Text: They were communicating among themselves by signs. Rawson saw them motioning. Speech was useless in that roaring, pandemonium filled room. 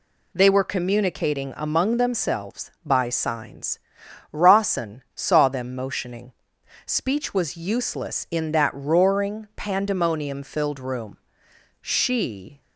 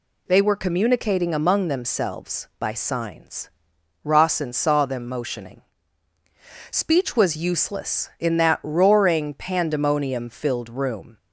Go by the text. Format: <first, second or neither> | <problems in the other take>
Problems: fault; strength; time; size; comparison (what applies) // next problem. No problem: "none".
second | goes on to say "She"; noticeable; from 11.8 s on; 0.80 s long